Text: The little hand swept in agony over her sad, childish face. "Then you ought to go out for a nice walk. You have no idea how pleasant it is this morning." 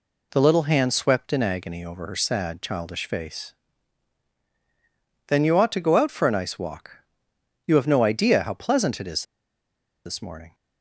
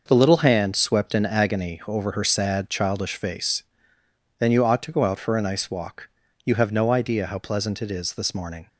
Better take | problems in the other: second | pauses between "is" and "this"; noticeable; at 9.2 s; 0.81 s long

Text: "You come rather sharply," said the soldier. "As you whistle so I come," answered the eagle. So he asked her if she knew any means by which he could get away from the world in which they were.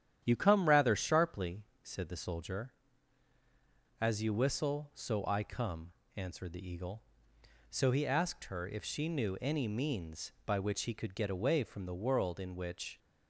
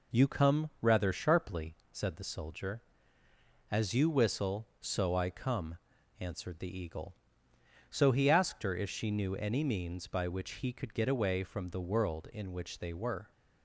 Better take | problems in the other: second | starts louder than the rest; strong; until 1.2 s; 10 dB // stops before "they were"; at 12.9 s

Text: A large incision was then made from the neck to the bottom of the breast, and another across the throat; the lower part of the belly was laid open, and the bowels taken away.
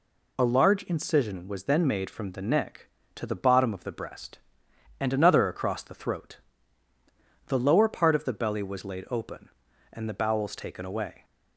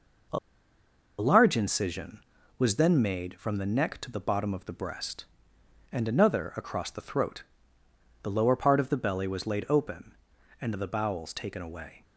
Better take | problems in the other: first | pauses between "A" and "large"; noticeable; at 0.3 s; 0.80 s long

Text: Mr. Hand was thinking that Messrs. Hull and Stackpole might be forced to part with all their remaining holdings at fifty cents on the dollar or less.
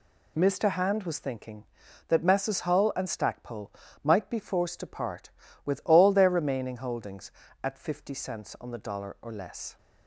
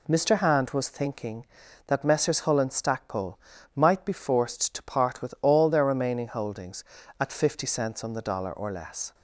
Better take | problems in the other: neither | pauses between "Stackpole" and "might"; slight; the same in both

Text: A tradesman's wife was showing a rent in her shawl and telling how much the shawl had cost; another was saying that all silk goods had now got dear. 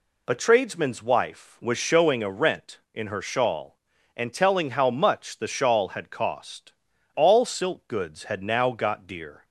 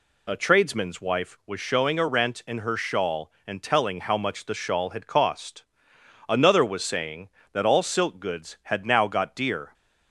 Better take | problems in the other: second | skips "another was saying that"; at 6.9 s

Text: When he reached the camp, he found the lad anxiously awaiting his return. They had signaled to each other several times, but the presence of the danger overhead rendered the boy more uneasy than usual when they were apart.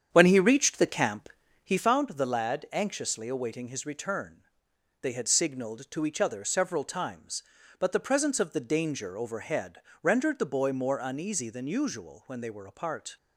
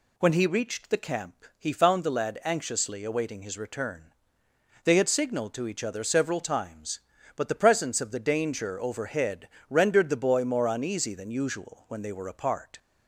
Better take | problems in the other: second | starts louder than the rest; strong; until 1.9 s; 8.5 dB // pauses between "overhead" and "rendered"; slight; at 9.8 s; 0.22 s long; slight in the second

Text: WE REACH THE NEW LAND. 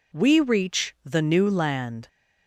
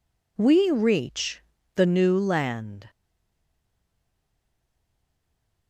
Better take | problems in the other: first | pauses between "REACH" and "THE"; slight; at 1.4 s; 0.34 s long // stays silent after the last word; strong; from 2.8 s on; 2.8 s long

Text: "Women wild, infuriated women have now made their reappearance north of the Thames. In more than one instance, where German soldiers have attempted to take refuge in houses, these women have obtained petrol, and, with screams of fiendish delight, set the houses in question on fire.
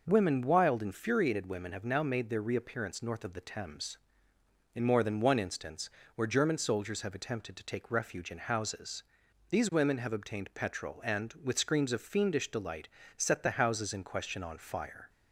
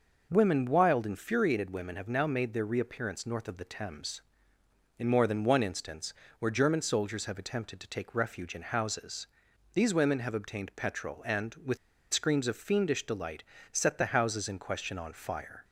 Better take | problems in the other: first | pauses between "with" and "screams"; at 11.7 s; 0.36 s long

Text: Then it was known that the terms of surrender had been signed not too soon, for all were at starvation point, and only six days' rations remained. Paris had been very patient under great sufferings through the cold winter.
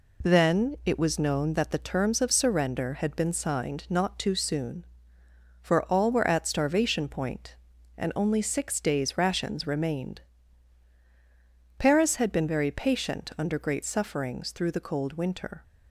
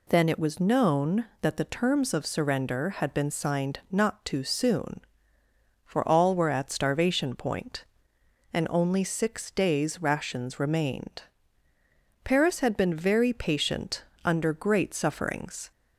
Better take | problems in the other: first | pauses between "patient" and "under"; slight; at 14.0 s; 0.22 s long // stops before "through the cold winter"; at 15.7 s

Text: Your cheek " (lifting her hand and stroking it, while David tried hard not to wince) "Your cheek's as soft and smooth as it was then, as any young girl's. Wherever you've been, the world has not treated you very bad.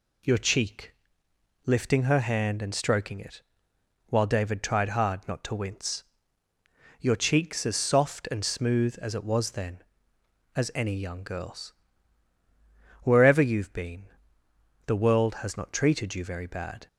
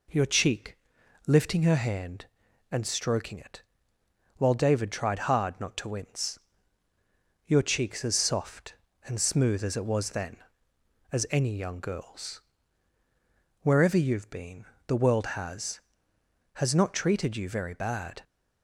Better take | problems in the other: first | says "has" twice; at 16.5 s

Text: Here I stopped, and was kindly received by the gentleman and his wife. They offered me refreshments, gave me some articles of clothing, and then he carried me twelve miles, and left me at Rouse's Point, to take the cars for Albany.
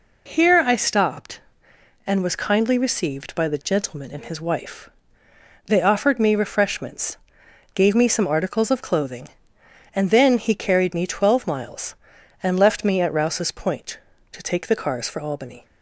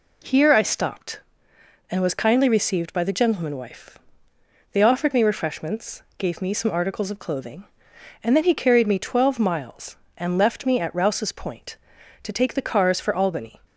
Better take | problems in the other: first | skips "and his"; at 3.5 s

